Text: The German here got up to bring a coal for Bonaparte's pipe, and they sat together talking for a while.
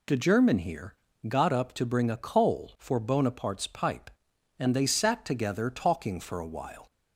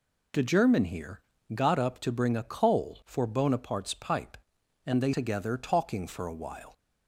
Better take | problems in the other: first | pauses between "here" and "got"; slight; at 1.2 s; 0.34 s long; slight in the first // skips "sat"; at 5.1 s

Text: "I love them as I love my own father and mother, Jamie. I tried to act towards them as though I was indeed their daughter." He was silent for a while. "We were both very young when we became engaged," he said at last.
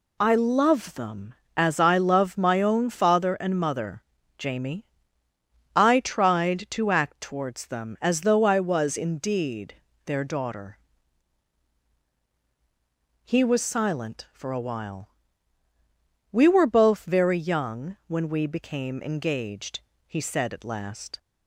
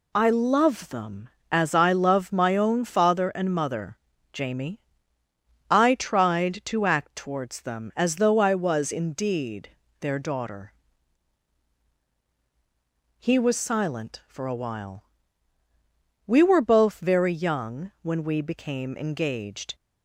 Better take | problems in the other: first | pauses between "indeed" and "their"; slight; at 9.6 s; 0.32 s long; slight in the first // stops before "he said at last"; at 19.7 s

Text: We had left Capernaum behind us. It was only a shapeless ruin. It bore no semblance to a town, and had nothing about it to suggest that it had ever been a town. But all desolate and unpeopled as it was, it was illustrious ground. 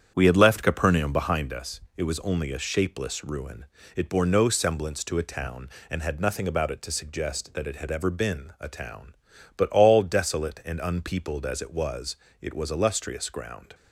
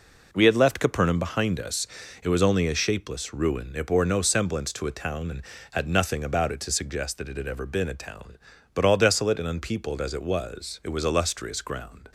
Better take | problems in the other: second | starts louder than the rest; strong; until 1.5 s; 8.5 dB

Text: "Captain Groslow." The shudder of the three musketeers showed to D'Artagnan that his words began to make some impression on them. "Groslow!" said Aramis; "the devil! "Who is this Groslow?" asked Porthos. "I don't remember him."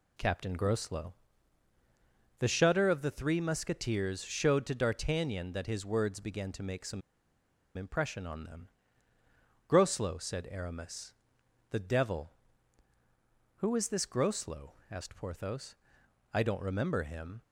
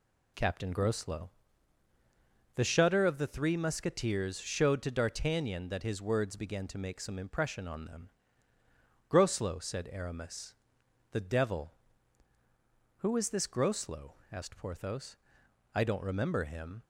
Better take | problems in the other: second | pauses between "some" and "impression"; noticeable; at 7.0 s; 0.76 s long

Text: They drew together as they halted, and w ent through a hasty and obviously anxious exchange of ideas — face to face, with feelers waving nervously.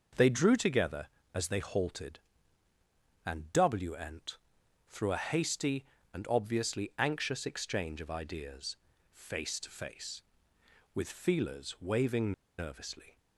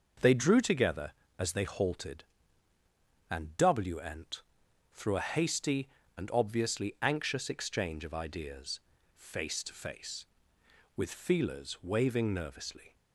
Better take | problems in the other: second | pauses between "ent" and "through"; noticeable; at 4.3 s; 0.50 s long; noticeable in the second // pauses between "waving" and "nervously"; slight; at 12.3 s; 0.26 s long

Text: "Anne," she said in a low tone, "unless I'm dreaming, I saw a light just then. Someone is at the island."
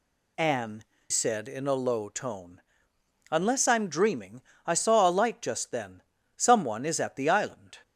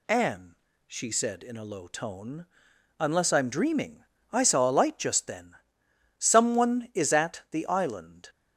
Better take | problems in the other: second | skips "she"; at 0.9 s

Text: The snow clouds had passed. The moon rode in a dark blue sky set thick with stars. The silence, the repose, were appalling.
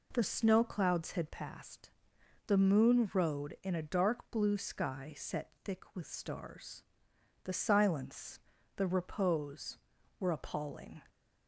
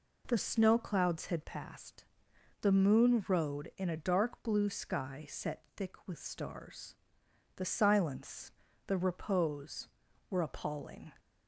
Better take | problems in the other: neither | none

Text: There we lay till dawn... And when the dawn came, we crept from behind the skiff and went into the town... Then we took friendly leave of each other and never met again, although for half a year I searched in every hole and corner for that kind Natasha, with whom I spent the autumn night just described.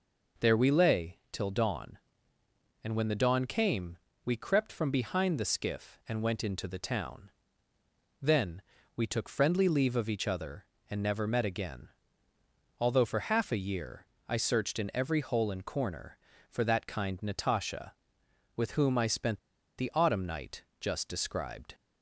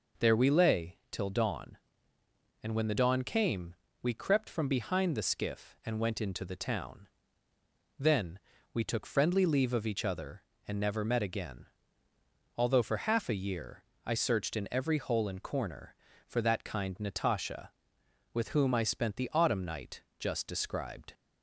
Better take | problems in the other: second | pauses between "Then" and "we"; slight; at 8.6 s; 0.34 s long; slight in the second // pauses between "year" and "I"; slight; at 14.0 s; 0.20 s long; slight in the second // pauses between "spent" and "the"; at 19.3 s; 0.37 s long // pauses between "night" and "just"; slight; at 20.6 s; 0.16 s long; slight in the second

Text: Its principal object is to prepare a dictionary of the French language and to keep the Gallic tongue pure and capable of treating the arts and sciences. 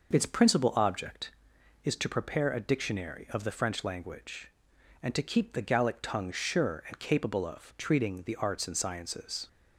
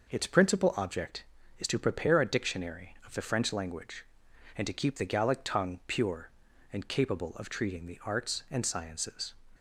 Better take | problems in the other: second | says "sure" for "pure"; at 6.3 s

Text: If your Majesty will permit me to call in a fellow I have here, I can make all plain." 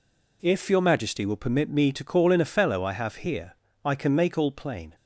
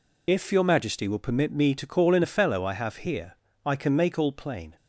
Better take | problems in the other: first | loses the start of "If"; at 0.2 s; 60 ms

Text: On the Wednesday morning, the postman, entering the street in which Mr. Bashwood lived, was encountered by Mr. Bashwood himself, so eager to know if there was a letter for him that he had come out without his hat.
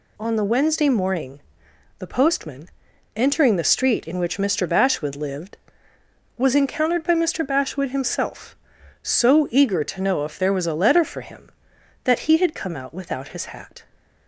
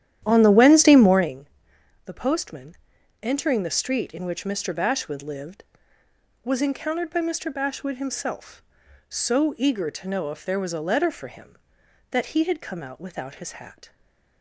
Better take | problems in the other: first | starts louder than the rest; strong; until 1.4 s; 11 dB // stays silent after the last word; slight; from 13.8 s on; 0.6 s long

